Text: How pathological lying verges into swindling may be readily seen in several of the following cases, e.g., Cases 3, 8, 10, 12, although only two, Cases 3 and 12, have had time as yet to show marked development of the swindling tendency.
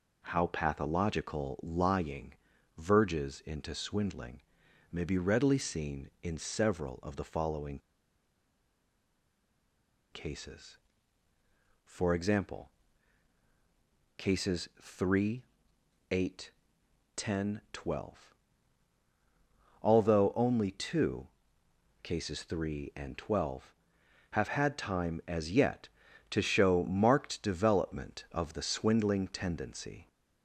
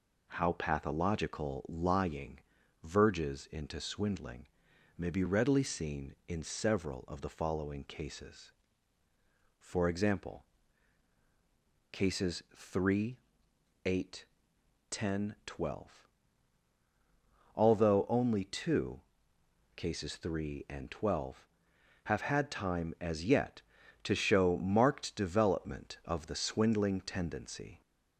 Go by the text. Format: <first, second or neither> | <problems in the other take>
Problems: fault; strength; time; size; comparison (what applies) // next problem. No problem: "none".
second | pauses between "lying" and "verges"; at 2.3 s; 0.42 s long; also in the second // pauses between "swindling" and "may"; noticeable; at 4.4 s; 0.50 s long; noticeable in the second // pauses between "following" and "cases"; strong; at 7.7 s; 2.3 s long